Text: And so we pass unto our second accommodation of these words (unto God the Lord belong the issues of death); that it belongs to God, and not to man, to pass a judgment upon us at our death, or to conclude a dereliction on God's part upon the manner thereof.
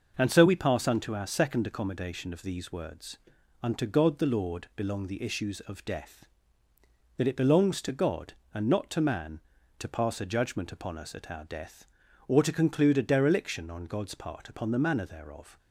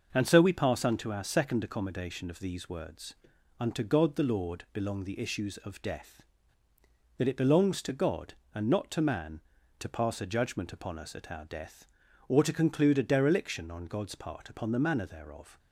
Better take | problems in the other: neither | starts louder than the rest; the same in both

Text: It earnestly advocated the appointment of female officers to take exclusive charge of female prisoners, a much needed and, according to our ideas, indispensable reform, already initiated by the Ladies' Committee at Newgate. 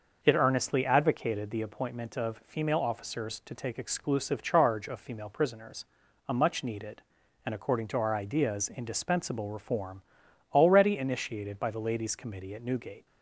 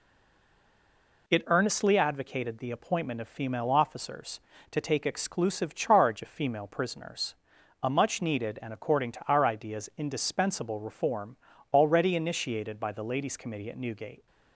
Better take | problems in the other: first | stays silent before the first word; noticeable; until 1.2 s; 1.2 s long

